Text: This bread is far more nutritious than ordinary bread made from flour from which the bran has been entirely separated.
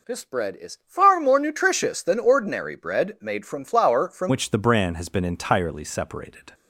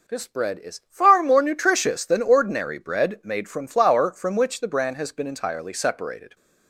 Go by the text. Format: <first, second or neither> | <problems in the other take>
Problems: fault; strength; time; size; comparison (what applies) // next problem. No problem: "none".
second | changes voice at "which"; from 4.2 s on; 2.3 s long